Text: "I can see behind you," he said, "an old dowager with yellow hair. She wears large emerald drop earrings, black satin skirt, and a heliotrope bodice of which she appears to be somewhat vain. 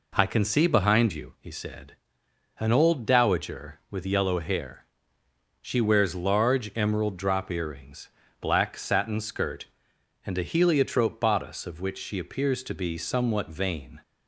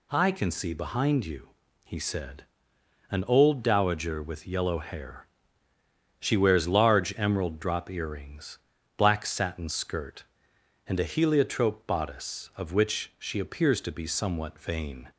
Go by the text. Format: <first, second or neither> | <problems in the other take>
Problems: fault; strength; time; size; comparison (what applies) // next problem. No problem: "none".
neither | none